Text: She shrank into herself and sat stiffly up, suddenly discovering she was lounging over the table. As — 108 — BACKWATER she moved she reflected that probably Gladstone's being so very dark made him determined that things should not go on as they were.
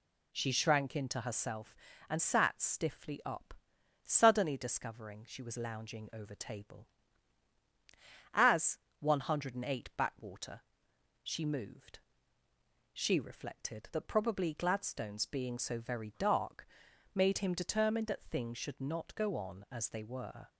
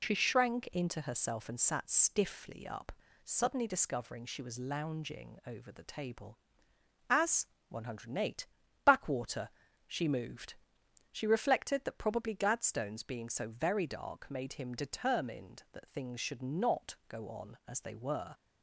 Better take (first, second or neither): second